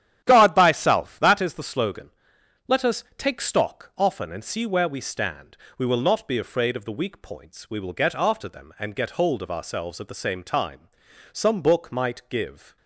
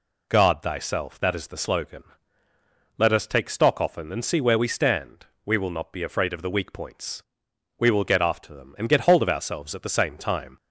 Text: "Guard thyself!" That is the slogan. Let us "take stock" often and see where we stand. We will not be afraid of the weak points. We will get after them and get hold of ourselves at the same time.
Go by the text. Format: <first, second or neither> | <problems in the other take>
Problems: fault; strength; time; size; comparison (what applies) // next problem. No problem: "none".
second | starts louder than the rest; strong; until 1.2 s; 10.5 dB // goes on to say "Some book might give"; from 11.3 s on; 1.4 s long